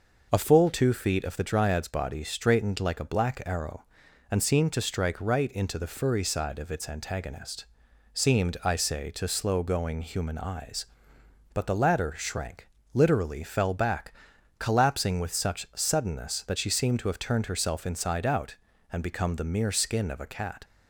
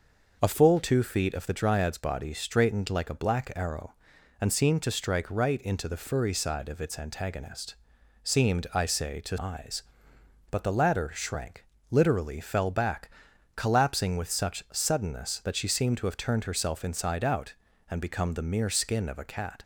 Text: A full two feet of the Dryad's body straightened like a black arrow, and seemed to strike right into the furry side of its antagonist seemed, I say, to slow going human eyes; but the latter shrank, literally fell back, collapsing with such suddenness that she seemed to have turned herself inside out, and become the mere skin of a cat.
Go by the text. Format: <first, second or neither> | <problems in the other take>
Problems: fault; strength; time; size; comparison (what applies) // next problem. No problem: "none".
first | pauses between "antagonist" and "seemed"; noticeable; at 7.7 s; 0.52 s long; noticeable in the first // skips "slow going human"; at 9.3 s